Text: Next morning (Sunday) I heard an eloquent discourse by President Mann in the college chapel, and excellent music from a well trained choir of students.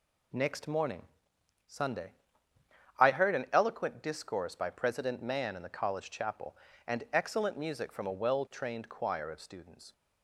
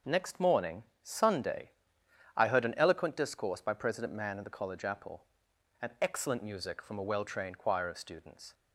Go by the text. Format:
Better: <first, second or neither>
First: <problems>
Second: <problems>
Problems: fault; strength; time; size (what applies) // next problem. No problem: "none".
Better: first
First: none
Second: starts louder than the rest; until 1.2 s; 6.5 dB // says "apple" for "chapel"; at 4.8 s